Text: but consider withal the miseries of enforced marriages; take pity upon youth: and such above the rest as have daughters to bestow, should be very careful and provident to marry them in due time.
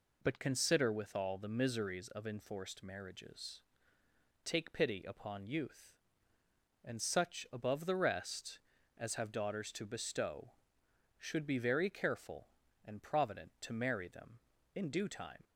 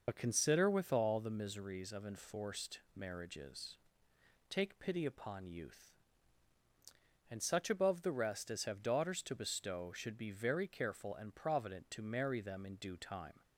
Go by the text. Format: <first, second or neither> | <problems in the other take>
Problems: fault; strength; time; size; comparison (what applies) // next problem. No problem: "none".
first | loses the start of "but"; at 0.0 s; 55 ms